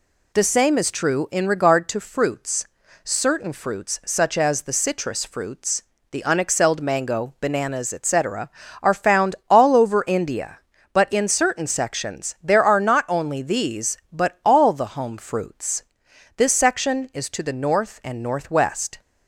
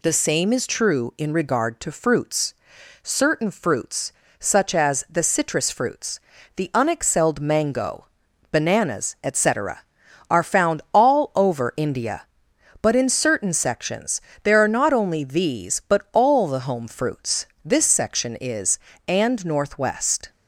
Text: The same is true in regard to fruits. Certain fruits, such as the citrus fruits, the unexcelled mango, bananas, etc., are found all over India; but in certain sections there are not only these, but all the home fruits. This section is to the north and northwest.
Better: first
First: none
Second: pauses between "sections" and "there"; slight; at 14.2 s; 0.22 s long // skips "to the north"; at 18.9 s

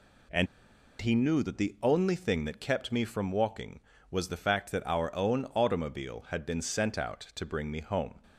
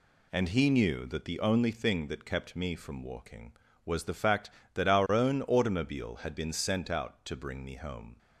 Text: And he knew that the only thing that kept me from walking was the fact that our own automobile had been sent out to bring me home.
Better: second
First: pauses between "And" and "he"; noticeable; at 0.4 s; 0.55 s long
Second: none

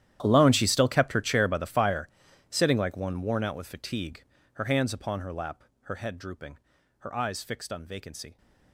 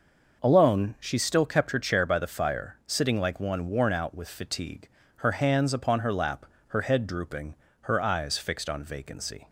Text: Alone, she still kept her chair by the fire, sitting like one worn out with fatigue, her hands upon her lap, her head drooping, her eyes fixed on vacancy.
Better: second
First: gets quieter; strong; throughout; 20 dB // starts louder than the rest; strong; until 1.2 s; 11.5 dB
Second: starts louder than the rest; noticeable; until 1.4 s; 6 dB

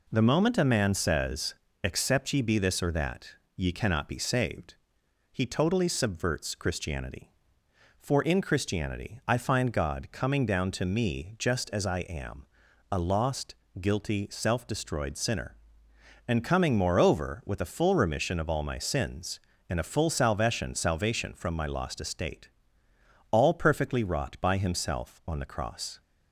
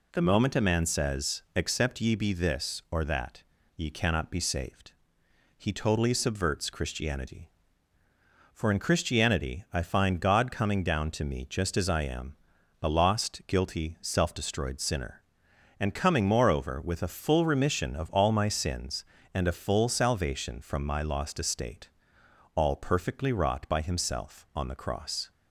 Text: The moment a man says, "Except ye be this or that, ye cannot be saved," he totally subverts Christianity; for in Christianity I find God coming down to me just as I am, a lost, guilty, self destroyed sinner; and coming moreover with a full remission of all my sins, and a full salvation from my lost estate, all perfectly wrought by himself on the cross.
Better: second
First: says "salvation" twice; at 20.7 s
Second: none

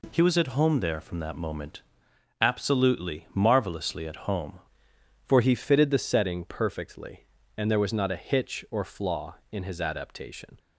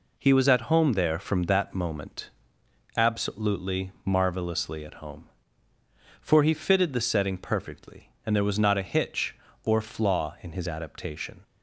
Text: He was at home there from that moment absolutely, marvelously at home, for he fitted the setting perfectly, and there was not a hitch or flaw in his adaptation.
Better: second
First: pauses between "moment" and "absolutely"; noticeable; at 1.8 s; 0.58 s long // changes voice at "for"; from 5.2 s on; 5.3 s long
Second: pauses between "moment" and "absolutely"; noticeable; at 2.3 s; 0.64 s long

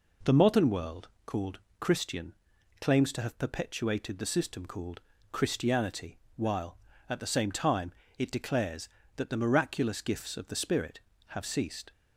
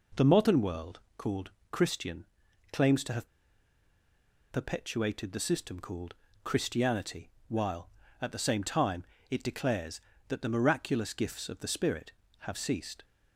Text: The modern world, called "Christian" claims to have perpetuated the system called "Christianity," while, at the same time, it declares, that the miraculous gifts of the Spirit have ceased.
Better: first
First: pauses between "called" and "Christian"; slight; at 1.5 s; 0.22 s long // pauses between "Christian" and "claims"; noticeable; at 2.3 s; 0.46 s long // pauses between "called" and "Christianity"; slight; at 4.9 s; 0.31 s long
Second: pauses between "called" and "Christian"; slight; at 1.4 s; 0.22 s long // pauses between "Christian" and "claims"; noticeable; at 2.2 s; 0.46 s long // pauses between "have" and "perpetuated"; strong; at 3.2 s; 1.2 s long // pauses between "called" and "Christianity"; slight; at 6.1 s; 0.30 s long

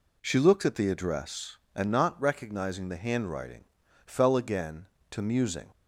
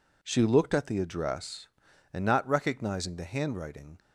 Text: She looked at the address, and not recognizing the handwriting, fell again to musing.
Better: first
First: none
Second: stops before "fell again to musing"; at 3.9 s

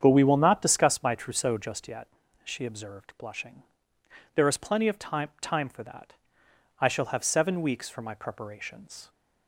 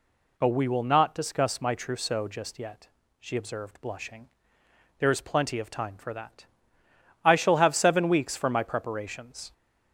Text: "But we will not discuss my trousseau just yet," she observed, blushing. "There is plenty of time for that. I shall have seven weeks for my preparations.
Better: second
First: starts louder than the rest; strong; until 1.0 s; 8 dB // says "time" twice; at 5.4 s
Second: none

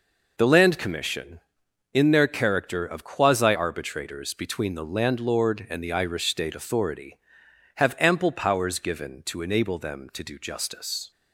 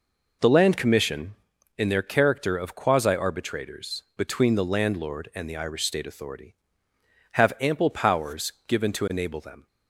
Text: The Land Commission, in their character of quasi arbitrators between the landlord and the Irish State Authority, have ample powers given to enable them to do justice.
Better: first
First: none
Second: pauses between "powers" and "given"; slight; at 8.5 s; 0.16 s long // stops before "to do justice"; at 9.6 s

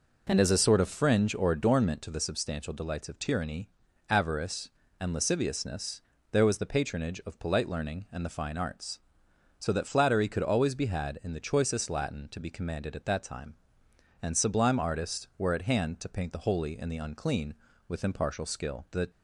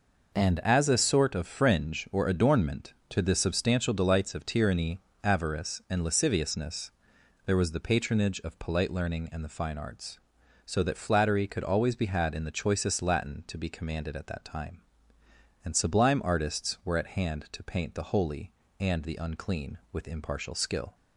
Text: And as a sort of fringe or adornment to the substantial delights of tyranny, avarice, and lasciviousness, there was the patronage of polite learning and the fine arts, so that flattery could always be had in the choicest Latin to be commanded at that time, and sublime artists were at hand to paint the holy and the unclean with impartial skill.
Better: second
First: goes on to say "The"; slight; from 18.8 s on; 0.18 s long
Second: none

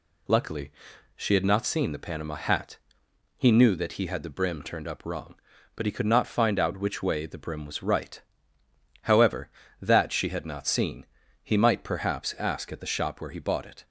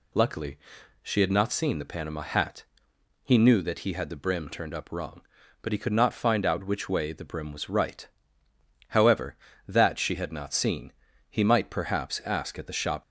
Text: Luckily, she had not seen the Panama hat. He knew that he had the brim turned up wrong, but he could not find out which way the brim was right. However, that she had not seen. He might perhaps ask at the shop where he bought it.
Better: first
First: none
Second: stops before "where he bought it"; at 13.0 s

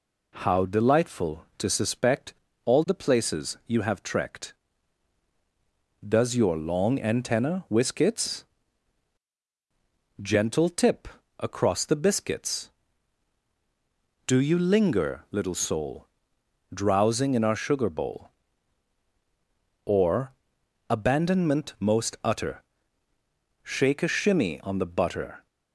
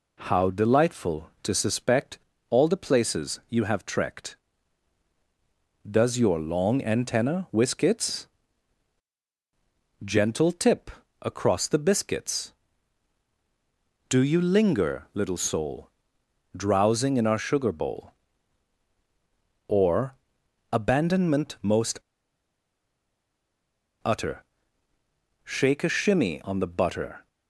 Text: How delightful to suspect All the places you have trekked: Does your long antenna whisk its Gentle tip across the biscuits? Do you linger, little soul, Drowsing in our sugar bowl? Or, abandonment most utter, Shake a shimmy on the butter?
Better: first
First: pauses between "suspect" and "All"; slight; at 2.3 s; 0.32 s long // pauses between "its" and "Gentle"; strong; at 8.4 s; 1.7 s long // pauses between "tip" and "across"; slight; at 11.0 s; 0.32 s long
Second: pauses between "suspect" and "All"; slight; at 2.1 s; 0.32 s long // pauses between "its" and "Gentle"; strong; at 8.2 s; 1.7 s long // pauses between "tip" and "across"; slight; at 10.9 s; 0.32 s long // pauses between "most" and "utter"; strong; at 22.0 s; 2.0 s long

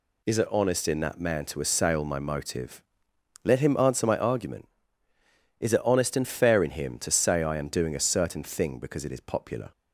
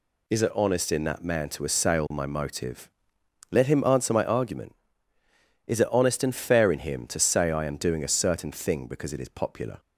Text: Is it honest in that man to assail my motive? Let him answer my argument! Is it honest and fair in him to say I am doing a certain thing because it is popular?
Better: neither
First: none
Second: none

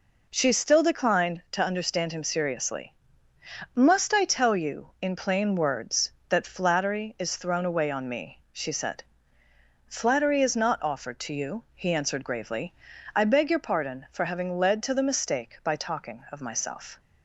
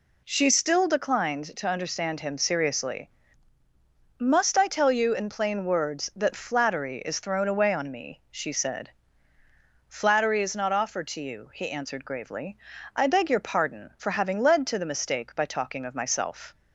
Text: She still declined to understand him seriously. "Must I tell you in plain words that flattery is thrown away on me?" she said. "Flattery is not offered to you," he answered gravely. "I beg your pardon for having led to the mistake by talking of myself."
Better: neither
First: none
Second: none

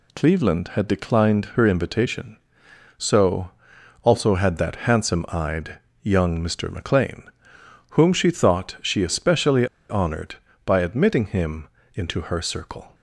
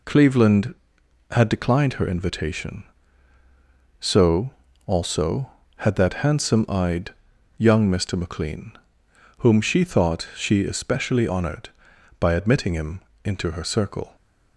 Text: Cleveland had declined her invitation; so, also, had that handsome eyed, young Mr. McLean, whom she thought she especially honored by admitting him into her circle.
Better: second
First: pauses between "especially" and "honored"; slight; at 9.6 s; 0.24 s long // pauses between "him" and "into"; slight; at 11.6 s; 0.26 s long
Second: pauses between "him" and "into"; slight; at 13.0 s; 0.22 s long

